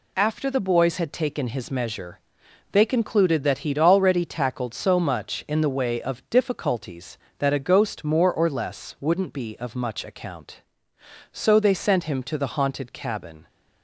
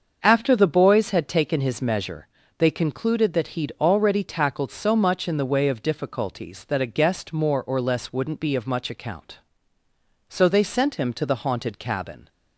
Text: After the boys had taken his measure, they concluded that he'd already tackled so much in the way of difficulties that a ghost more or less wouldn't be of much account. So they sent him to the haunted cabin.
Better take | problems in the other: first | starts louder than the rest; until 1.2 s; 6.5 dB // says "guest" for "ghost"; at 6.8 s

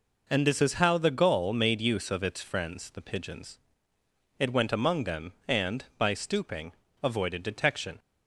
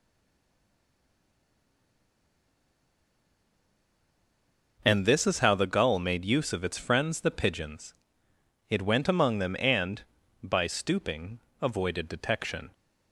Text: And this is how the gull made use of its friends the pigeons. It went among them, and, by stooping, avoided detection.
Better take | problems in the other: first | stays silent before the first word; strong; until 4.7 s; 4.7 s long

